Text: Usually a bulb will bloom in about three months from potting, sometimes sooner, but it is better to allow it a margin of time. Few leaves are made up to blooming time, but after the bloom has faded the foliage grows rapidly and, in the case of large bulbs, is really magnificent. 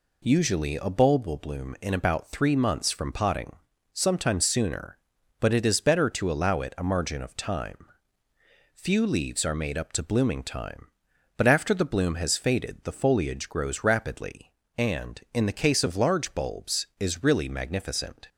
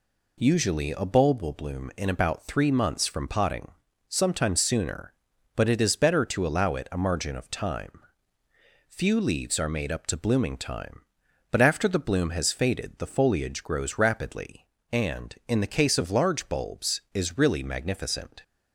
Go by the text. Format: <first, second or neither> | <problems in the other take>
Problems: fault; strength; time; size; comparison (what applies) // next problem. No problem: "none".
neither | none